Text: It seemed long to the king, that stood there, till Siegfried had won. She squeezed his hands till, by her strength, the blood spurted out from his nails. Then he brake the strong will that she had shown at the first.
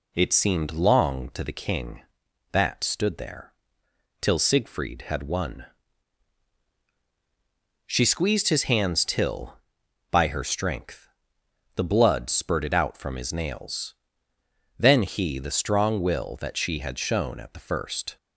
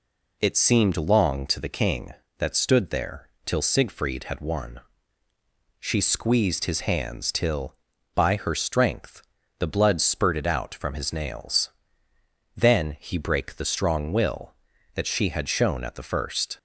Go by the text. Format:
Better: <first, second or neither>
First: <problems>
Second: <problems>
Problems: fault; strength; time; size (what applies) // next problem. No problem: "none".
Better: second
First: skips "brake"; at 15.3 s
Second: none